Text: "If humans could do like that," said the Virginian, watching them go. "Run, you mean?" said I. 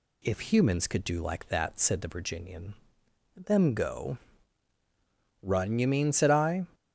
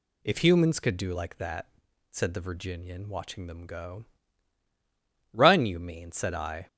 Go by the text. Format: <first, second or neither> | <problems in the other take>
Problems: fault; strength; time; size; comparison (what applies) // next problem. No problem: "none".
second | skips "watching"; at 3.0 s